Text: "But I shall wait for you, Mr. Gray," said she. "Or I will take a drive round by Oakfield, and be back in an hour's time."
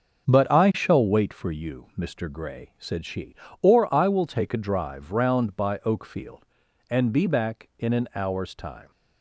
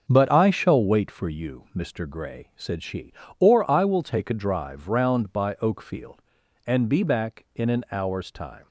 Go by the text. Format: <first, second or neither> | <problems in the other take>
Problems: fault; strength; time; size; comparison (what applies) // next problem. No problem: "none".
neither | starts louder than the rest; the same in both